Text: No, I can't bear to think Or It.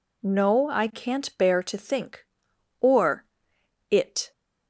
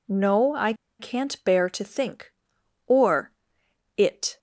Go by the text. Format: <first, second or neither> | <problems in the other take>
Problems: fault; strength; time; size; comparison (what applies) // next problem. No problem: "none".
first | pauses between "I" and "can't"; slight; at 0.7 s; 0.26 s long // pauses between "Or" and "It"; noticeable; at 3.3 s; 0.66 s long; noticeable in the first